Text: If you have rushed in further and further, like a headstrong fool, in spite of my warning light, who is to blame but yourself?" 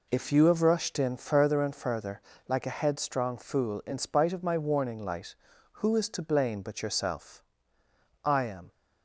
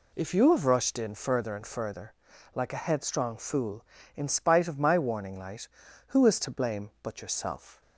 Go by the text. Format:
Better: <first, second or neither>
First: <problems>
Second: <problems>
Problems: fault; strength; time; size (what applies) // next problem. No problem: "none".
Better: second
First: goes on to say "I am"; slight; from 8.2 s on; 0.46 s long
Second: none